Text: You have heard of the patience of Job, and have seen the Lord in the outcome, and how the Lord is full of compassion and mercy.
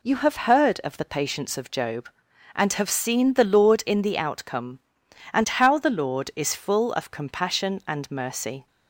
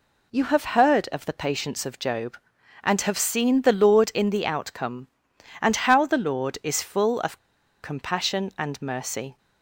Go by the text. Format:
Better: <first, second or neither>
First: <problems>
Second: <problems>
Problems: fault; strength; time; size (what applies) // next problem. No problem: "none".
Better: first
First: none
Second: pauses between "of" and "compassion"; at 7.3 s; 0.43 s long